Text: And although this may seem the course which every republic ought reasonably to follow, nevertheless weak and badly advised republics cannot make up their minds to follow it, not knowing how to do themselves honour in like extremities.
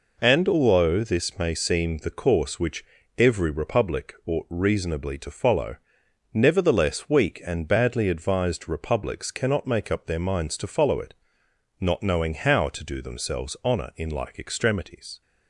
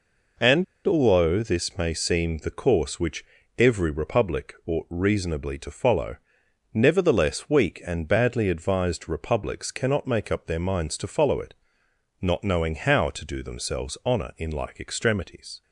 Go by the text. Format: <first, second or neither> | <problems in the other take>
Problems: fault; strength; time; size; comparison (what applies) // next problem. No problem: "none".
first | pauses between "And" and "although"; slight; at 0.6 s; 0.22 s long // pauses between "which" and "every"; slight; at 3.2 s; 0.34 s long; slight in the first